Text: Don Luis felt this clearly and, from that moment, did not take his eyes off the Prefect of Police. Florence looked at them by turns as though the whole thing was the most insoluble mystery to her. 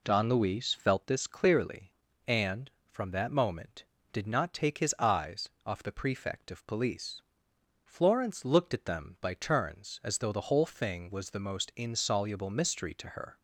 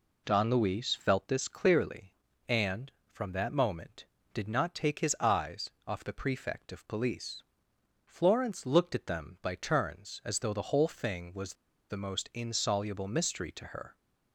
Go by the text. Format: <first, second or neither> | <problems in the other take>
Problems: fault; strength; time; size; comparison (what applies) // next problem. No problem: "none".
first | pauses between "eyes" and "off"; slight; at 5.6 s; 0.18 s long; slight in the first // pauses between "was" and "the"; at 11.5 s; 0.36 s long